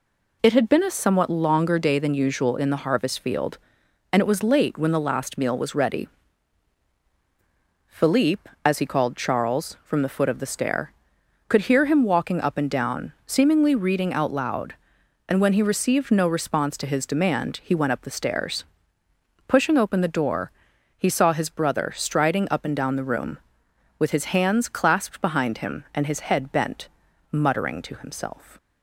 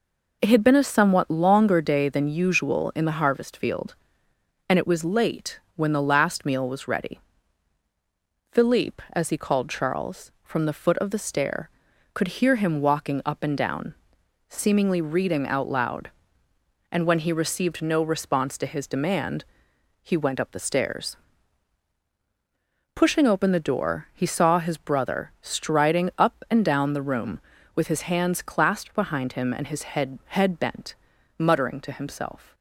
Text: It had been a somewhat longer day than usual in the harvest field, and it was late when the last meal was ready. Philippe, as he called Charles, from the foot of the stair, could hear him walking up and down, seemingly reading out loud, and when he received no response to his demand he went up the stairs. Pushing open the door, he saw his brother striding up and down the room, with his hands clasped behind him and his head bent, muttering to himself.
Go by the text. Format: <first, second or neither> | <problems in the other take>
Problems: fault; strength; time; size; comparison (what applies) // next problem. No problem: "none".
first | pauses between "late" and "when"; slight; at 5.5 s; 0.16 s long // pauses between "demand" and "he"; noticeable; at 19.4 s; 0.58 s long // says "head" twice; at 30.2 s